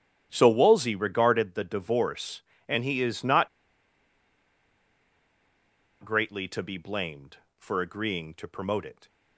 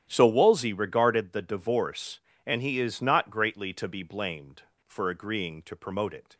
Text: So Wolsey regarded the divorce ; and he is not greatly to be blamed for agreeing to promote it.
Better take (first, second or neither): second